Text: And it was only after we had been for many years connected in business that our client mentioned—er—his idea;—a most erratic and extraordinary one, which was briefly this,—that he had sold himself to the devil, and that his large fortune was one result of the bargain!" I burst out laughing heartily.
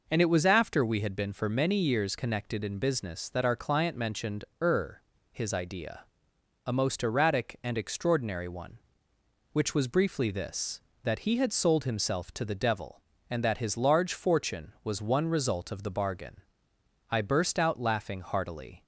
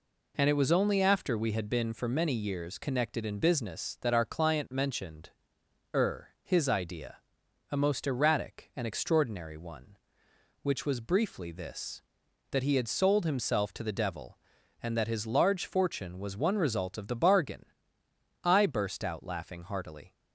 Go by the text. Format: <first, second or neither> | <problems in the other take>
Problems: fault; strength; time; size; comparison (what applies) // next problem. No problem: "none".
second | skips "only"; at 0.4 s